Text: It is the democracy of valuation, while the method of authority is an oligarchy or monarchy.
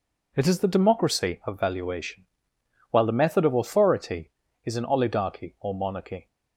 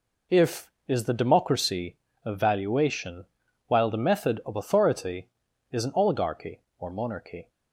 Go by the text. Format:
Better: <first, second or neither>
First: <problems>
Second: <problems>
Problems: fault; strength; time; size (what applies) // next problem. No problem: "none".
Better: first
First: none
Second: says "If" for "It"; at 0.3 s